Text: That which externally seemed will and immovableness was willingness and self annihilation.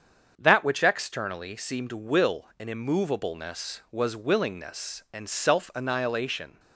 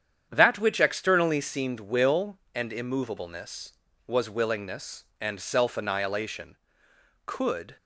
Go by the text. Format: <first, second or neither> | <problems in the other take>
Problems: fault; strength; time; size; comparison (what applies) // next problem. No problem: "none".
first | starts louder than the rest; strong; until 1.3 s; 8.5 dB; strong in the first // goes on to say "Could"; from 7.2 s on; 0.50 s long